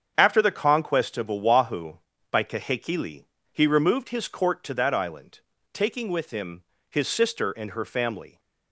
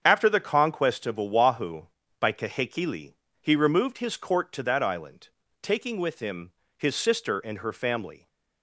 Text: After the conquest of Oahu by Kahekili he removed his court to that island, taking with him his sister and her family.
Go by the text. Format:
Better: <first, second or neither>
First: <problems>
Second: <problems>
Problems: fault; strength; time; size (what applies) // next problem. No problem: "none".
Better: neither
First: starts louder than the rest; strong; until 1.1 s; 7.5 dB // pauses between "Kahekili" and "he"; slight; at 3.2 s; 0.26 s long // pauses between "him" and "his"; slight; at 6.6 s; 0.26 s long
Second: starts louder than the rest; strong; until 1.0 s; 7.5 dB // pauses between "Kahekili" and "he"; slight; at 3.1 s; 0.26 s long // pauses between "him" and "his"; slight; at 6.5 s; 0.24 s long